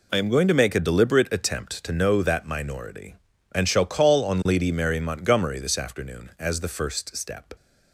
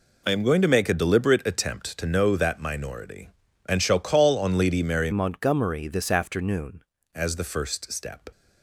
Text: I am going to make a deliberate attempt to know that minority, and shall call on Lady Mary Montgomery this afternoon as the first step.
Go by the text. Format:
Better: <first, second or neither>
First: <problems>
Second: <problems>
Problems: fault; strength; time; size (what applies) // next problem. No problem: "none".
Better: first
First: none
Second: changes voice from "Montgomery" to "afternoon"; from 5.1 to 6.8 s; 1.7 s long